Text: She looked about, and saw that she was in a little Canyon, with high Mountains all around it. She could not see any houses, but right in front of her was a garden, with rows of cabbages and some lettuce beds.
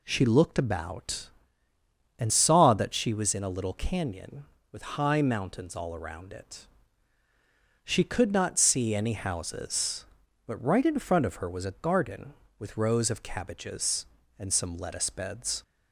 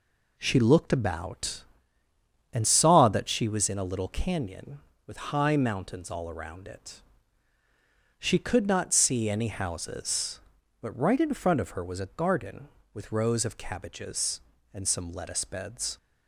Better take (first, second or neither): first